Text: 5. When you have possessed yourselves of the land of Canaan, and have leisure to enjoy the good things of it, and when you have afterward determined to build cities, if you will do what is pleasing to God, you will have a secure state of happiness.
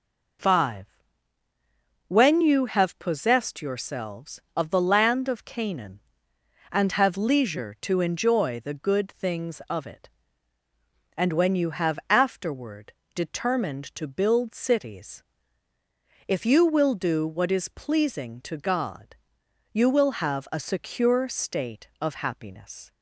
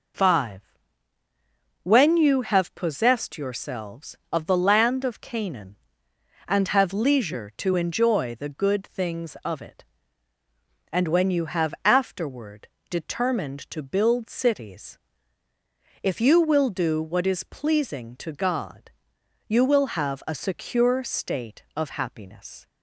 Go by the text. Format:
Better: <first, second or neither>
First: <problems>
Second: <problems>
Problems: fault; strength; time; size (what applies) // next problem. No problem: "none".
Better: neither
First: pauses between "afterward" and "determined"; slight; at 12.9 s; 0.20 s long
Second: pauses between "afterward" and "determined"; slight; at 12.6 s; 0.20 s long